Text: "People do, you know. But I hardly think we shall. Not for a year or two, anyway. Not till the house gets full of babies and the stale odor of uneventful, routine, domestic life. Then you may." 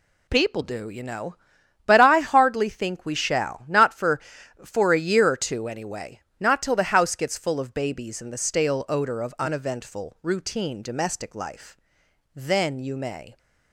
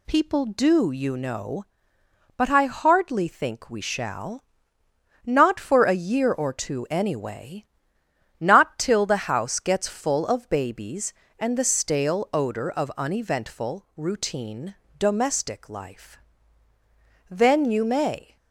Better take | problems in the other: second | says "for" twice; at 4.6 s

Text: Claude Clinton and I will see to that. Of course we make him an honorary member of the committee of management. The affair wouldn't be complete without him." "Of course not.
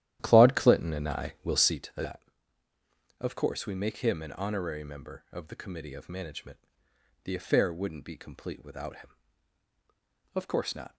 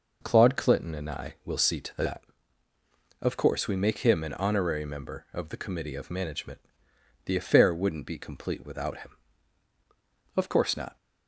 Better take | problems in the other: second | starts louder than the rest; strong; until 1.8 s; 12 dB

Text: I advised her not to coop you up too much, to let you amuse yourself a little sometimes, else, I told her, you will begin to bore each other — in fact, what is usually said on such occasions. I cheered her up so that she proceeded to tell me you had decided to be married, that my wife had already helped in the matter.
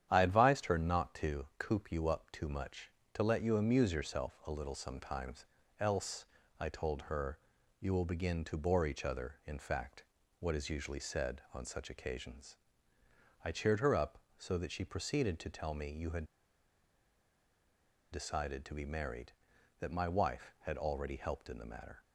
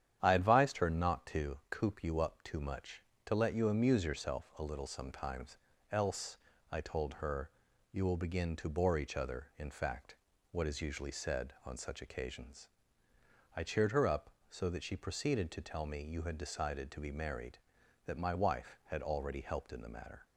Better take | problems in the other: second | starts louder than the rest; strong; until 1.1 s; 10 dB; strong in the second // pauses between "had" and "decided"; strong; at 16.2 s; 1.8 s long

